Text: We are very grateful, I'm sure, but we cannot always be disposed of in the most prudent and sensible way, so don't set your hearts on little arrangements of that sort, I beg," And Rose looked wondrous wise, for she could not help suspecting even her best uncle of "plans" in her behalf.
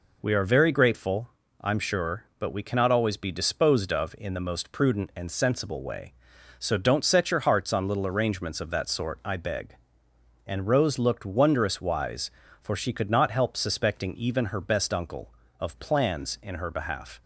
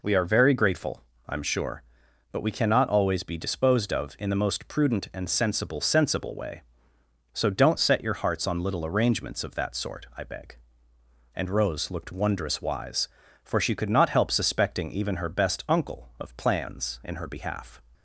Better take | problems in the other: first | says "sensible" twice; at 5.8 s

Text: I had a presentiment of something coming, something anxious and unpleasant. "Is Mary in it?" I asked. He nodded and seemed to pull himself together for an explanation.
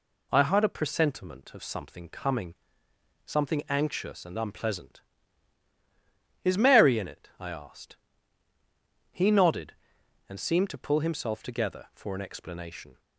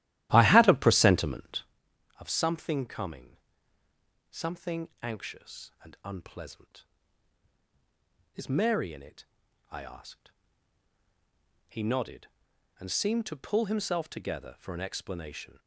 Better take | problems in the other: first | starts louder than the rest; strong; until 1.7 s; 13.5 dB // pauses between "something" and "anxious"; slight; at 4.8 s; 0.16 s long

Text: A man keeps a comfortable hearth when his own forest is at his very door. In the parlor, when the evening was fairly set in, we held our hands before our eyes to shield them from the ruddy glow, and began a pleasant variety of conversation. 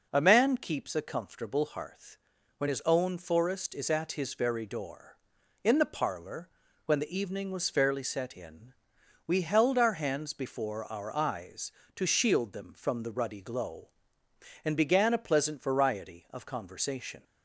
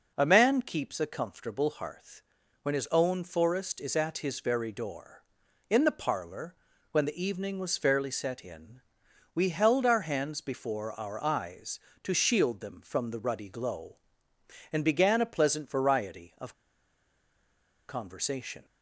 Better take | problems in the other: first | pauses between "hearth" and "when"; at 2.2 s; 0.40 s long; also in the first // pauses between "of" and "conversation"; strong; at 16.5 s; 1.3 s long

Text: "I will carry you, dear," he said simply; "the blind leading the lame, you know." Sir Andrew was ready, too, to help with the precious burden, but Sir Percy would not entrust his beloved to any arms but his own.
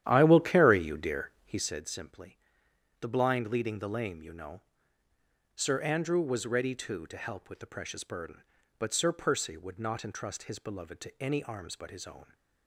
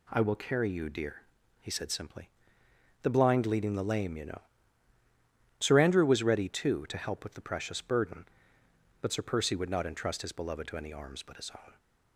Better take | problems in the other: second | starts louder than the rest; strong; until 1.8 s; 11 dB

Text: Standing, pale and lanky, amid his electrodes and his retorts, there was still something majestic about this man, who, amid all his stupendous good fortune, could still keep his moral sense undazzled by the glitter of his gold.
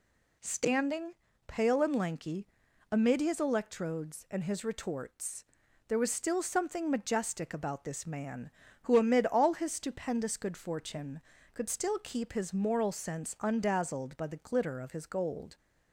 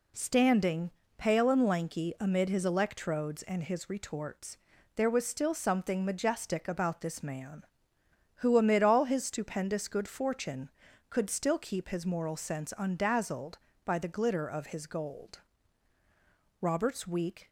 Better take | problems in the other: first | goes on to say "Robert's weak"; noticeable; from 16.6 s on; 0.88 s long

